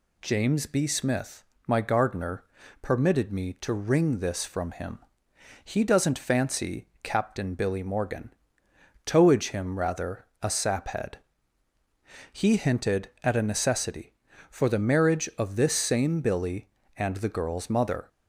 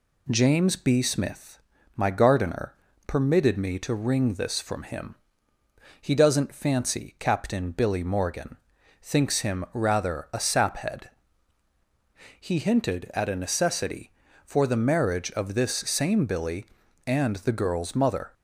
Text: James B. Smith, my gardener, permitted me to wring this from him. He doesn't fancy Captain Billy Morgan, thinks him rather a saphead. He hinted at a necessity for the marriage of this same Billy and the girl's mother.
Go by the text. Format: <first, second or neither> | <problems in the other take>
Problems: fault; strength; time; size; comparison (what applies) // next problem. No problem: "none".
second | pauses between "fancy" and "Captain"; slight; at 6.8 s; 0.16 s long // says "towage" for "thinks"; at 9.0 s // pauses between "rather" and "a"; slight; at 10.2 s; 0.16 s long